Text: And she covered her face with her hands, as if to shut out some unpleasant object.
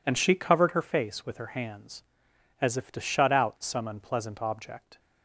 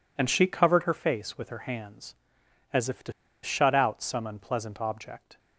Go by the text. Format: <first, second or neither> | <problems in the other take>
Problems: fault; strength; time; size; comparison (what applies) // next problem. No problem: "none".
first | pauses between "to" and "shut"; slight; at 3.1 s; 0.31 s long